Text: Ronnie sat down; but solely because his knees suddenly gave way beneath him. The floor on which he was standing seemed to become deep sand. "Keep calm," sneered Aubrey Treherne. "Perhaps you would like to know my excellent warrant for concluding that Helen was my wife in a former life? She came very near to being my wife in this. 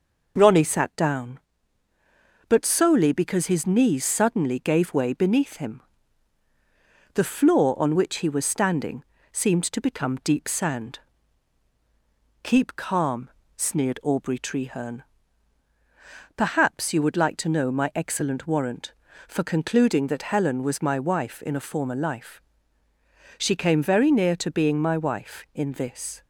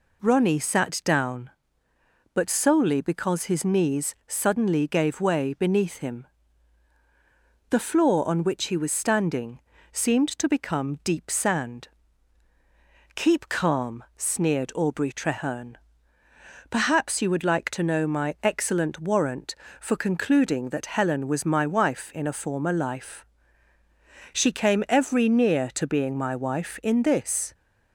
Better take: first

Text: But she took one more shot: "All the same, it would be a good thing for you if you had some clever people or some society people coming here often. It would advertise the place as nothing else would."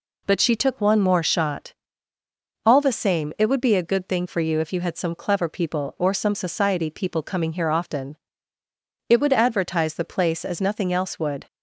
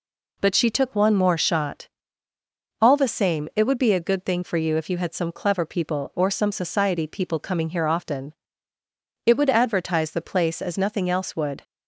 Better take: neither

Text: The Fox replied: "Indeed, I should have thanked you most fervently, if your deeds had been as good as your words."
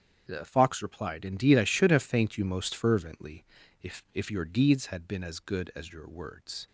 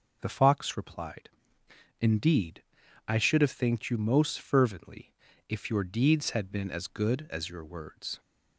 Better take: second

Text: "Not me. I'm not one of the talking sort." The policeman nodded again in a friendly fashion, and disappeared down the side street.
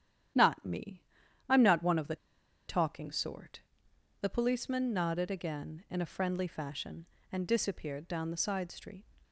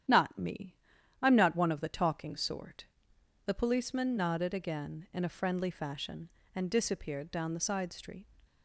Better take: second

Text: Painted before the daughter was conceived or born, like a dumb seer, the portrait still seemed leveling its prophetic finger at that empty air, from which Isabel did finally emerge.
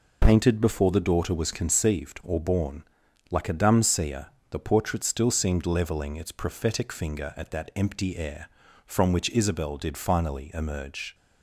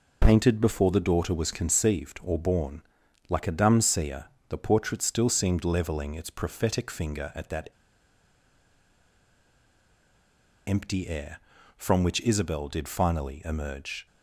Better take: first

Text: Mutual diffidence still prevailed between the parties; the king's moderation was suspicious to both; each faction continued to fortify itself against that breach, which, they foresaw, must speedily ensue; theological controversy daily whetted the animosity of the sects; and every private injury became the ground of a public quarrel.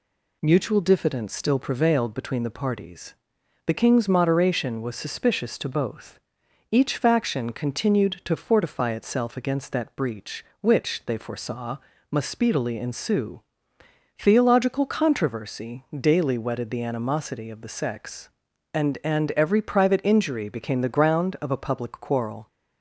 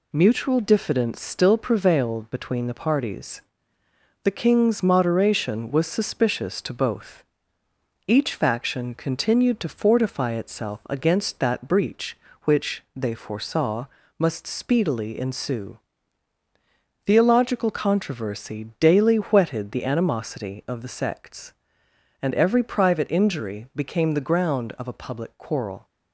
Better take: second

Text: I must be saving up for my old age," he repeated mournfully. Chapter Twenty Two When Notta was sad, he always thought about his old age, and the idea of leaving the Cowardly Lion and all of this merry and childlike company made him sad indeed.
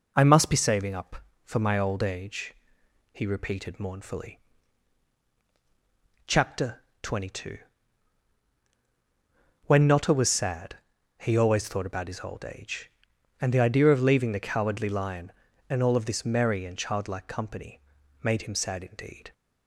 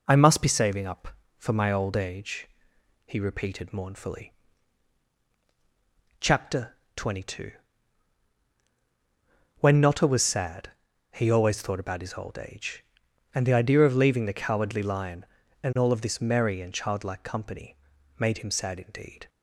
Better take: neither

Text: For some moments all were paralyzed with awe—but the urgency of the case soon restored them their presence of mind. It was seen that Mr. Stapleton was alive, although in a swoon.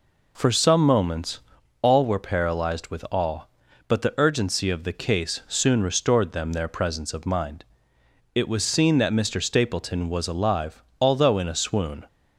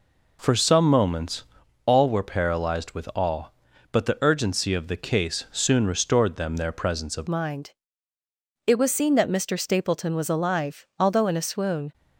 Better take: first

